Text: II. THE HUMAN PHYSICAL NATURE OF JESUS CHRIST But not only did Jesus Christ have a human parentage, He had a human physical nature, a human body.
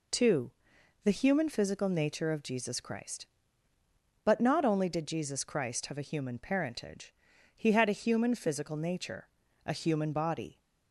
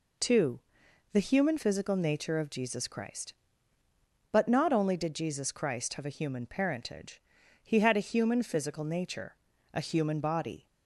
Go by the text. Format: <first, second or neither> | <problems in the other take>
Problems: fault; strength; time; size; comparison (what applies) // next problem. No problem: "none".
neither | none